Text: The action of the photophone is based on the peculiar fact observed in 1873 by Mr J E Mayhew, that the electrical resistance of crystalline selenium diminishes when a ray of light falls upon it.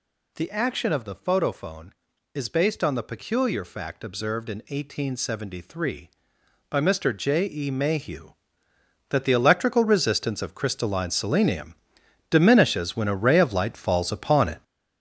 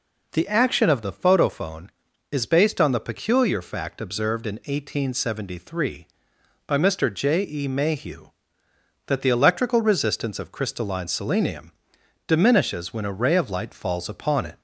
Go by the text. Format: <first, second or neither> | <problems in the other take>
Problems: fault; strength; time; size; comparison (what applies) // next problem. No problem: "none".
second | gets louder; strong; throughout; 7.5 dB // pauses between "selenium" and "diminishes"; noticeable; at 11.7 s; 0.56 s long; noticeable in the second